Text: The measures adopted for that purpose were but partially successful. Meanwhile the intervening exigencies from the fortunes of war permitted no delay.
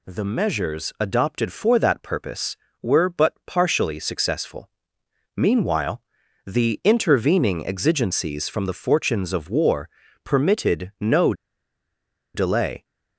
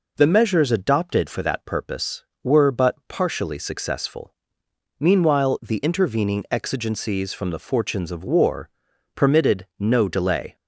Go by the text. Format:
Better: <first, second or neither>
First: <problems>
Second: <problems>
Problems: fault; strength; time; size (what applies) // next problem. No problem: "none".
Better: second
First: pauses between "Meanwhile" and "the"; at 6.0 s; 0.44 s long // pauses between "war" and "permitted"; at 9.8 s; 0.38 s long // pauses between "no" and "delay"; at 11.3 s; 1.0 s long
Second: pauses between "war" and "permitted"; noticeable; at 8.6 s; 0.46 s long